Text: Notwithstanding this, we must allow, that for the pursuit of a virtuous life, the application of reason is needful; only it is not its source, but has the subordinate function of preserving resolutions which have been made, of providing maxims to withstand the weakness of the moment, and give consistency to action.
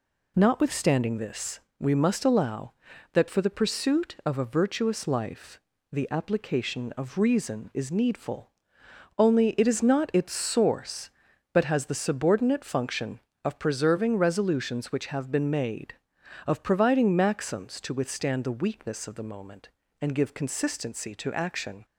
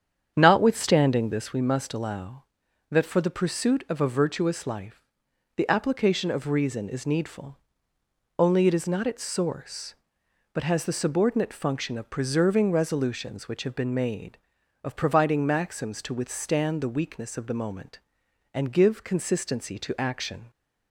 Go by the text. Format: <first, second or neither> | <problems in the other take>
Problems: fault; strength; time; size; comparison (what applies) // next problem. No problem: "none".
first | starts louder than the rest; strong; until 1.5 s; 8 dB